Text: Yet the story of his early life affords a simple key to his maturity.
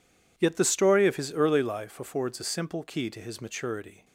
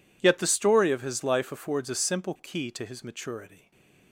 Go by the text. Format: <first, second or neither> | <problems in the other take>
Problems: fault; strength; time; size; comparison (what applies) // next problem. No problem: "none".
first | skips "early"; at 1.2 s // stays silent after the last word; slight; from 3.5 s on; 0.6 s long